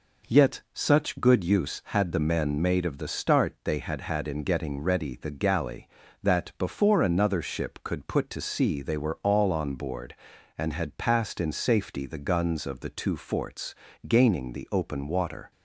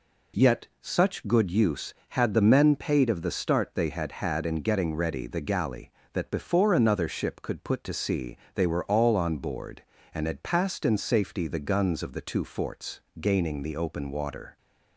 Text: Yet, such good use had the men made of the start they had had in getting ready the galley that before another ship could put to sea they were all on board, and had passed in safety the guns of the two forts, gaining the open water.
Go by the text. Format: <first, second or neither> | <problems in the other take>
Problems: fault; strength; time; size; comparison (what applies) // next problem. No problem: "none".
first | says "paid" for "made"; at 2.7 s // pauses between "sea" and "they"; slight; at 8.3 s; 0.18 s long